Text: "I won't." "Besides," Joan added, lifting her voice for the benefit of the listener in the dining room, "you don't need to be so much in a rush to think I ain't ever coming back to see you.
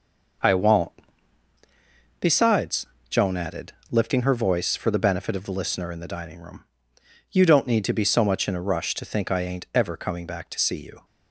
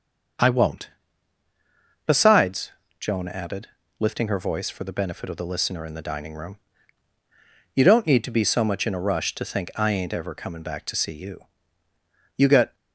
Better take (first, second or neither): first